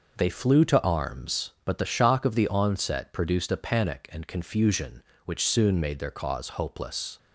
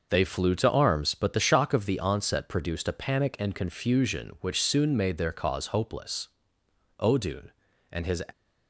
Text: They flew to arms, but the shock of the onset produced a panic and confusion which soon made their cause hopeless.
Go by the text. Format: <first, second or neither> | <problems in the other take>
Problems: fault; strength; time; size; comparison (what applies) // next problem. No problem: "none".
first | goes on to say "Odun and his"; noticeable; from 6.9 s on; 1.2 s long